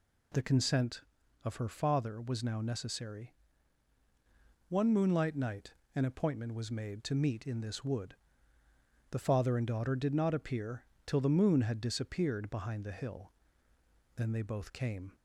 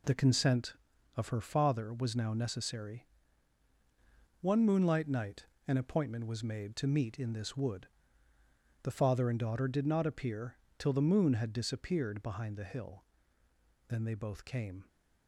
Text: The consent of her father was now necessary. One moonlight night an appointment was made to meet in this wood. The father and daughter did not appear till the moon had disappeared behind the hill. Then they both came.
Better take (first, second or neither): first